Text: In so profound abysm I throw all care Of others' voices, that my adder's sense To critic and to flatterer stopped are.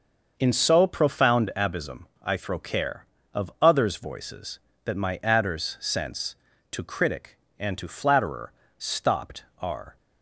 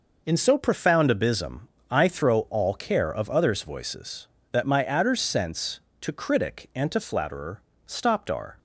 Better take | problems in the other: second | starts louder than the rest; until 1.3 s; 6 dB // pauses between "abysm" and "I"; slight; at 2.0 s; 0.18 s long; slight in the second // skips "all"; at 2.5 s // pauses between "flatterer" and "stopped"; slight; at 8.5 s; 0.24 s long; slight in the second

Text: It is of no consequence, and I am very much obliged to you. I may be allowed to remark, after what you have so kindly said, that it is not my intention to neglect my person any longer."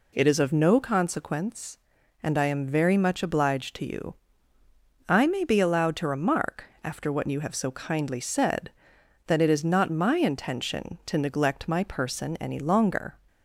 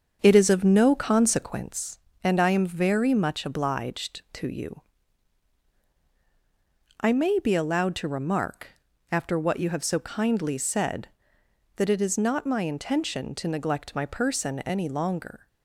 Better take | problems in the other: first | starts louder than the rest; until 1.7 s; 7 dB

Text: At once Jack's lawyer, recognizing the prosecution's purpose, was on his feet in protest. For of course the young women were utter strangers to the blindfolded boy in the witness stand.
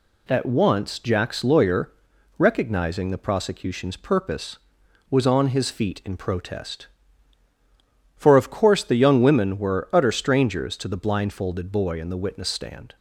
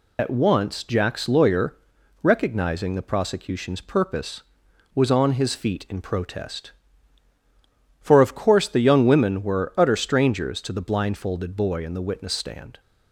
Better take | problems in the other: first | loses the start of "At"; at 0.1 s; 65 ms

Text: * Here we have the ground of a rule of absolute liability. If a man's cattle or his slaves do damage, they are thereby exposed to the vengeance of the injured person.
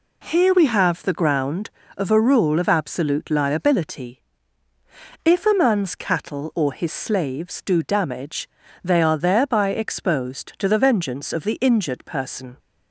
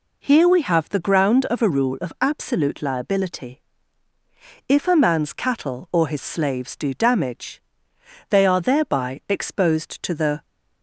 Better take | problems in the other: first | stops before "vengeance of the injured person"; at 10.4 s

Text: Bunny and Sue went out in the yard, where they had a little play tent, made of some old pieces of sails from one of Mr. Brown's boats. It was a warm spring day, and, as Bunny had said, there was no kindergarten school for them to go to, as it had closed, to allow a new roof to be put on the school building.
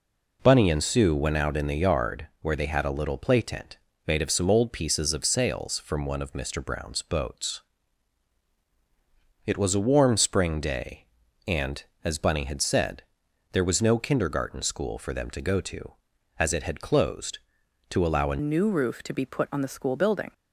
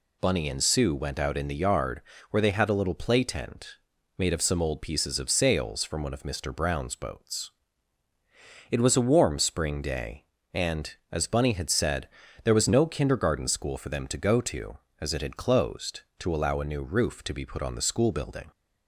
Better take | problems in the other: second | changes voice at "new"; from 18.4 s on; 1.9 s long

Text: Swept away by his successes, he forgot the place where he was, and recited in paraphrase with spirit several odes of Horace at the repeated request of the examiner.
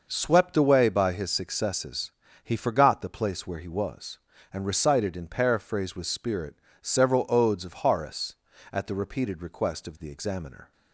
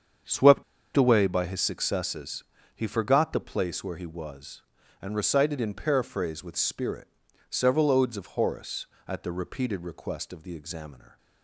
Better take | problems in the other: first | starts louder than the rest; strong; until 1.5 s; 7.5 dB // pauses between "Swept" and "away"; slight; at 0.6 s; 0.31 s long // pauses between "spirit" and "several"; at 7.0 s; 0.40 s long; slight in the first

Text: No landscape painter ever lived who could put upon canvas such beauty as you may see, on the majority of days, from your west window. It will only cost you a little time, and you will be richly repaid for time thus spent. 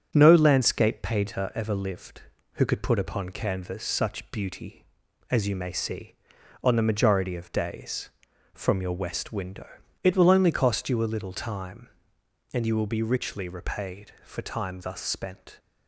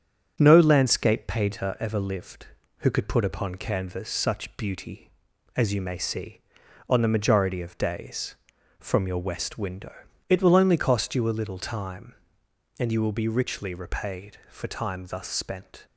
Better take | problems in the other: neither | starts louder than the rest; strong; the same in both

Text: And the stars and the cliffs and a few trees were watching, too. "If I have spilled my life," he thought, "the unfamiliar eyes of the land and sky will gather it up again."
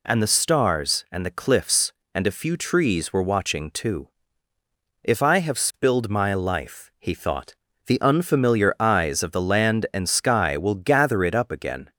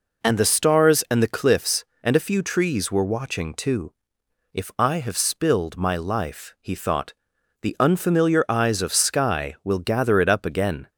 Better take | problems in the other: first | skips "the land and"; at 9.0 s

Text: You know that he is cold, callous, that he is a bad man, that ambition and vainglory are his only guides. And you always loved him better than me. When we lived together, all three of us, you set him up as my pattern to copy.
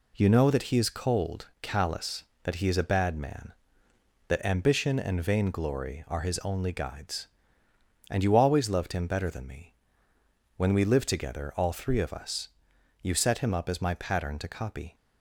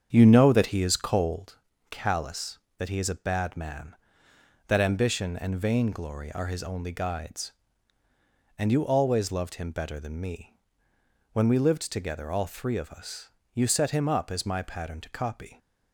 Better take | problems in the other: first | starts louder than the rest; strong; until 1.5 s; 7.5 dB

